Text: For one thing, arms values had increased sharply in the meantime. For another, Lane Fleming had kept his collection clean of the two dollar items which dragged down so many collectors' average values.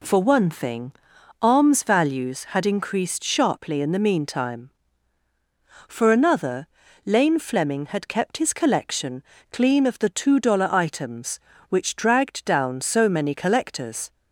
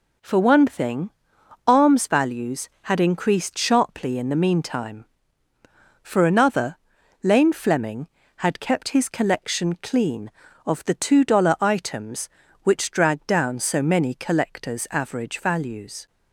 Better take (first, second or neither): second